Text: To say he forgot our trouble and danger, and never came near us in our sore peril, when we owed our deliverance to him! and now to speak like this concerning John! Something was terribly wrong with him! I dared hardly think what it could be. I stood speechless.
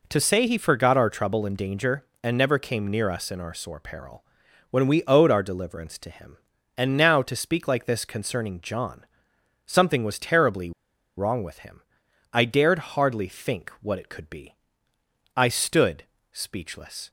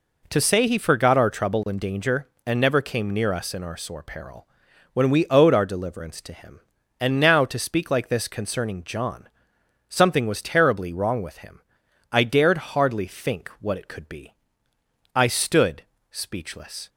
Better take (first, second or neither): second